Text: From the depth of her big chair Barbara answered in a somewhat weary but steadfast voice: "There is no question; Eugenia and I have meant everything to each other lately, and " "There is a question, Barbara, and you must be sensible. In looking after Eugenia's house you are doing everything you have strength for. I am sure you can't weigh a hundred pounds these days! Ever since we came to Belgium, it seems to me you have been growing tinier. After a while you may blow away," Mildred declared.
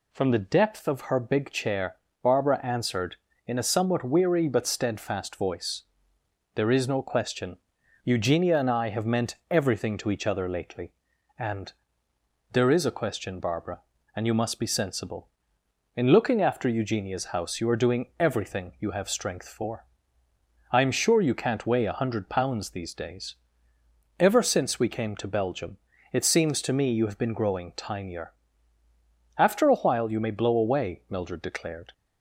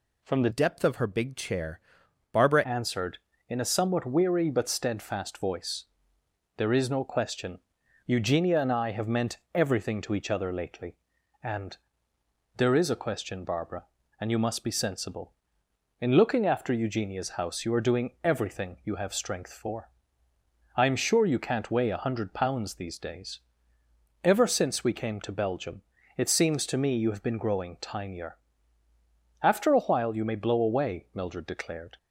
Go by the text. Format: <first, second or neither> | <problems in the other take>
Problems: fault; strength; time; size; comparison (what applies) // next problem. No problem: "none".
first | changes voice from "depth" to "Barbara"; from 0.5 to 2.6 s; 2.1 s long // pauses between "chair" and "Barbara"; noticeable; at 1.8 s; 0.52 s long; slight in the first // pauses between "meant" and "everything"; slight; at 9.3 s; 0.16 s long